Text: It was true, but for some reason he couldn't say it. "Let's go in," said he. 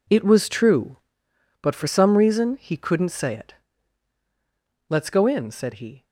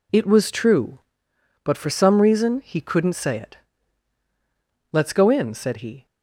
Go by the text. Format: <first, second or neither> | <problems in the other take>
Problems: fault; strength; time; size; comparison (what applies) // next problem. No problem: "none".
second | gets quieter; strong; throughout; 12 dB